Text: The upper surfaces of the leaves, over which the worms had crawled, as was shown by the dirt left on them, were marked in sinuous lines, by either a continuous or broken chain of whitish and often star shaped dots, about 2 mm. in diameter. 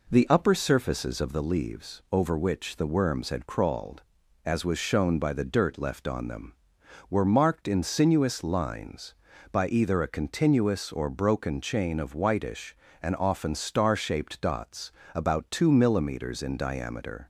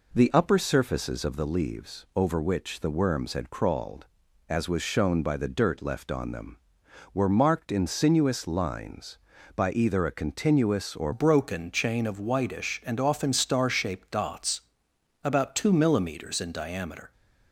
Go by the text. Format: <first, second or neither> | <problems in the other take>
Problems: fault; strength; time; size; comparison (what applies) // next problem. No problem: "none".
first | changes voice at "broken"; from 11.1 s on; 6.0 s long